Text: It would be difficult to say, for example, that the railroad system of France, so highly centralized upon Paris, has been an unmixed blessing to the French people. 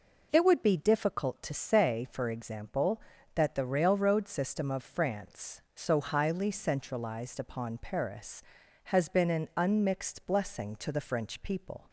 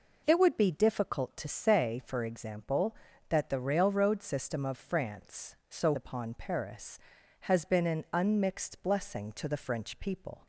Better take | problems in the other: first | skips "highly centralized"; at 5.9 s

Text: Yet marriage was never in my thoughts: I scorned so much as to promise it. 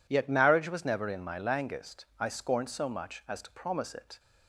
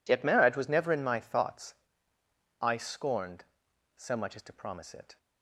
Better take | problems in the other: second | says "langest" for "thoughts"; at 1.3 s

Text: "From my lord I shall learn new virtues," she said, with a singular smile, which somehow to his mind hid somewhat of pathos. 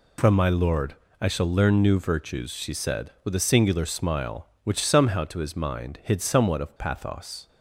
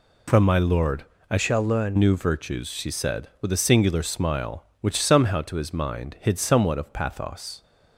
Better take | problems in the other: first | pauses between "lord" and "I"; slight; at 1.0 s; 0.26 s long; slight in the first // changes voice from "shall" to "learn"; from 1.3 to 1.9 s; 0.6 s long

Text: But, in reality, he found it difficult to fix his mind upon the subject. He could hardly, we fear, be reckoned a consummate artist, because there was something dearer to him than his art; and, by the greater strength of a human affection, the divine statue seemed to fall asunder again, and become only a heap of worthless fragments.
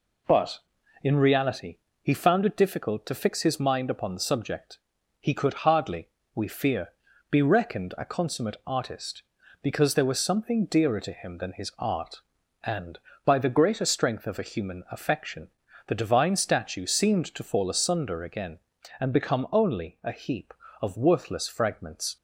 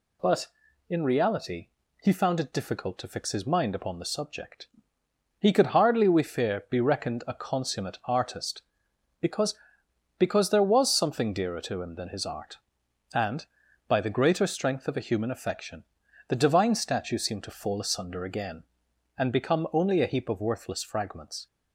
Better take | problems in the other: first | says "because" twice; at 10.1 s

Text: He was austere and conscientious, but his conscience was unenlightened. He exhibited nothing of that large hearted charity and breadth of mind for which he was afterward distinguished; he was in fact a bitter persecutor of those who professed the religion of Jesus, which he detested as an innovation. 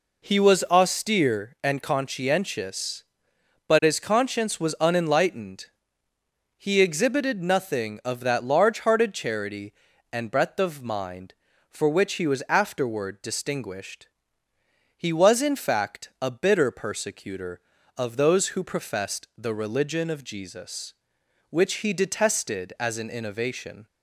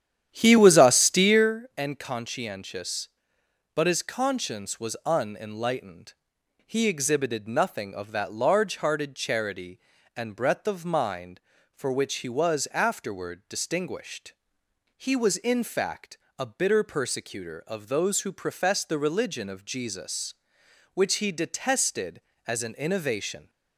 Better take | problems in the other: first | starts louder than the rest; strong; until 1.6 s; 10 dB // pauses between "fact" and "a"; slight; at 16.1 s; 0.22 s long

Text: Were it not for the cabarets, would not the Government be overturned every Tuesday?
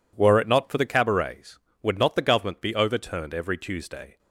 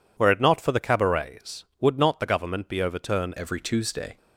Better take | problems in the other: first | changes voice at "every"; from 3.3 s on; 0.8 s long

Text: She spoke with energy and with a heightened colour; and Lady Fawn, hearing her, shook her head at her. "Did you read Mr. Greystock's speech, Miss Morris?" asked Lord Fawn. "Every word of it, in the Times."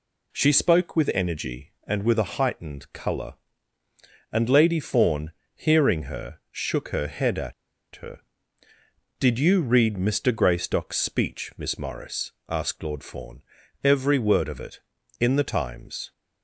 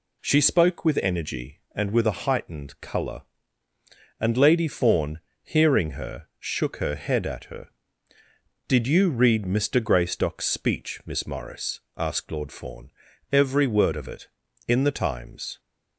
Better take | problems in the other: second | pauses between "at" and "her"; at 7.5 s; 0.42 s long

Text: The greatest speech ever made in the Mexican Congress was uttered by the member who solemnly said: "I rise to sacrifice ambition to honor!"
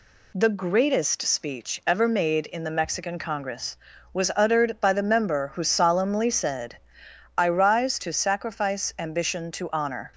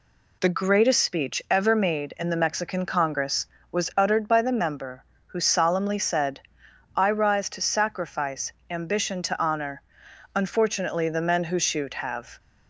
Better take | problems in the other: first | pauses between "sacrifice" and "ambition"; slight; at 8.5 s; 0.18 s long // goes on to say "Unfortunately the men who shoot have"; strong; from 10.3 s on; 2.0 s long

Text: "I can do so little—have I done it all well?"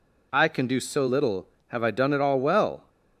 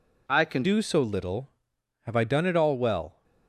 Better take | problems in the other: first | changes voice at "do"; from 0.6 s on; 2.6 s long

